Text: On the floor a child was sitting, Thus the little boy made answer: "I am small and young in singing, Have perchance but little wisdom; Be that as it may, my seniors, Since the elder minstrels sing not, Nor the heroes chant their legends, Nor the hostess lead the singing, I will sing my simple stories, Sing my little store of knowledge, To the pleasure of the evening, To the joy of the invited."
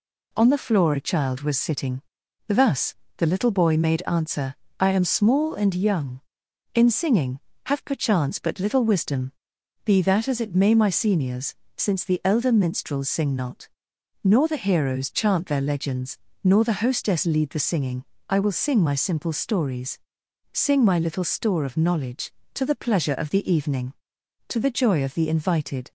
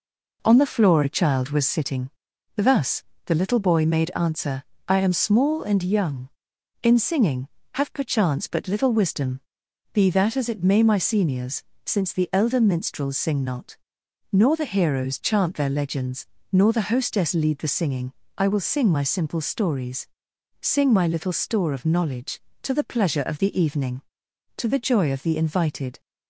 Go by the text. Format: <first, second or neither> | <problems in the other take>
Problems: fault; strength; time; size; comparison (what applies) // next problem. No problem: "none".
first | starts louder than the rest; noticeable; until 1.9 s; 4 dB // pauses between "Thus" and "the"; slight; at 3.0 s; 0.22 s long; slight in the first